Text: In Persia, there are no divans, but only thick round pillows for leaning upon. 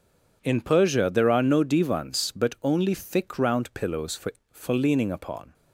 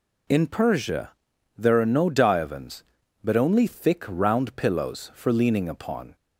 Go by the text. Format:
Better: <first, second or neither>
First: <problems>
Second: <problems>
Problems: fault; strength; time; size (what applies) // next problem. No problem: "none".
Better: second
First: says "for" twice; at 4.5 s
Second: none